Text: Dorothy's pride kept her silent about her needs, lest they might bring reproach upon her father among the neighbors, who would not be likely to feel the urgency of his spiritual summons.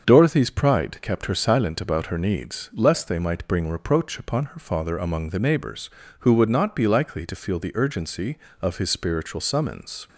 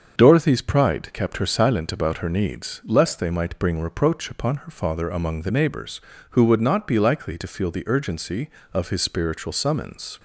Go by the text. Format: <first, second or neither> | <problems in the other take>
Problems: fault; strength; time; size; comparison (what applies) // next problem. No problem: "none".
neither | starts louder than the rest; the same in both